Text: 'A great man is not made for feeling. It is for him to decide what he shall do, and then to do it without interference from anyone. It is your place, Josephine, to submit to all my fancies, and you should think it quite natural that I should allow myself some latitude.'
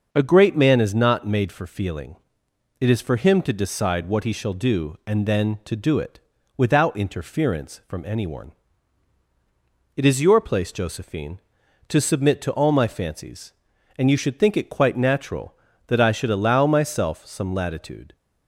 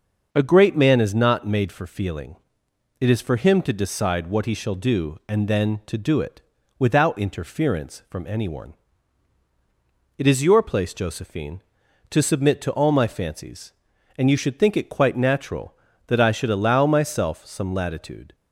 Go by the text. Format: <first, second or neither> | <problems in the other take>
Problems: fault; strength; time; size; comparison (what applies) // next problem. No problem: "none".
neither | starts louder than the rest; noticeable; the same in both // pauses between "it" and "without"; the same in both